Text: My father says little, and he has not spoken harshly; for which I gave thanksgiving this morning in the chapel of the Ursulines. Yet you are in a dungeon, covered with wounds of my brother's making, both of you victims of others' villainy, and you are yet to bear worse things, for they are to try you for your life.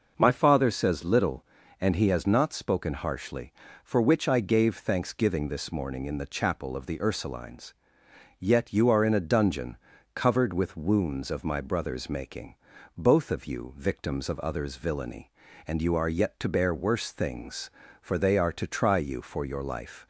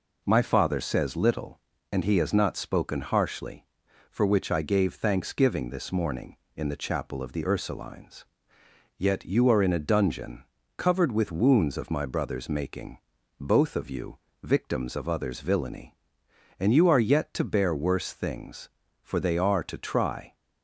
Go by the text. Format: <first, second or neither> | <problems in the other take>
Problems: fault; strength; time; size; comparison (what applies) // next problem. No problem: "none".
first | pauses between "you" and "victims"; slight; at 14.1 s; 0.26 s long // stops before "you for your life"; at 20.3 s